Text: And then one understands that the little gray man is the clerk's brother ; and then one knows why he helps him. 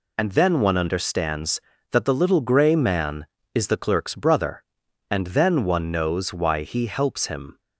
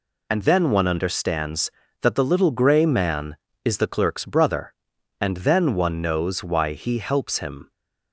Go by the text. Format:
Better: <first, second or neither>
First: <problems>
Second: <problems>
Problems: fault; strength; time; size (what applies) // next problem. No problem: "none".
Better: neither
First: none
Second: none